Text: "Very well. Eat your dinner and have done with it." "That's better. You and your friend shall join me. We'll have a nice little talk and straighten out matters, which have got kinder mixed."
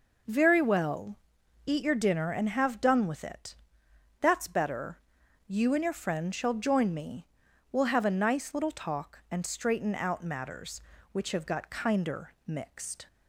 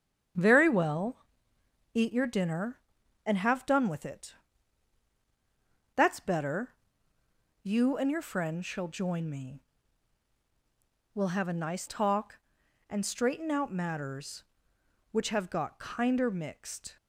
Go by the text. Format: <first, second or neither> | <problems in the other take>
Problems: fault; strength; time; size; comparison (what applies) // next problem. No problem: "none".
first | starts louder than the rest; strong; until 2.0 s; 8.5 dB // skips "little"; at 11.8 s